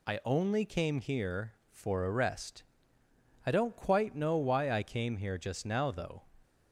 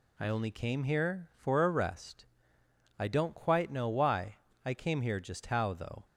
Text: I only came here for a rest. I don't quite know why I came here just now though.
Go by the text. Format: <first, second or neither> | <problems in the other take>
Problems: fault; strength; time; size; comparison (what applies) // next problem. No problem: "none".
first | pauses between "why" and "I"; slight; at 4.3 s; 0.28 s long // says "how" for "now"; at 5.4 s